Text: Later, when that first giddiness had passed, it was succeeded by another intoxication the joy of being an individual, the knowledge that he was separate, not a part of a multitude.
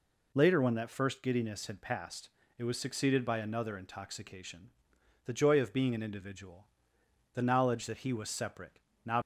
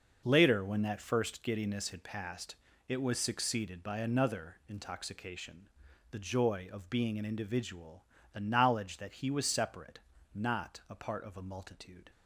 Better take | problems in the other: second | pauses between "intoxication" and "the"; noticeable; at 4.7 s; 0.54 s long; noticeable in the second // stops before "a part of a multitude"; at 9.2 s

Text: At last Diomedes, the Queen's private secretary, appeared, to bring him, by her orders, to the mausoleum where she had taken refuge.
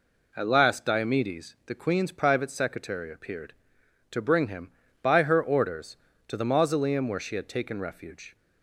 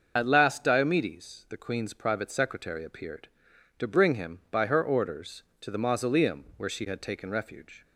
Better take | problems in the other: first | loses the start of "At"; at 0.1 s; 60 ms // starts louder than the rest; until 1.1 s; 6.5 dB

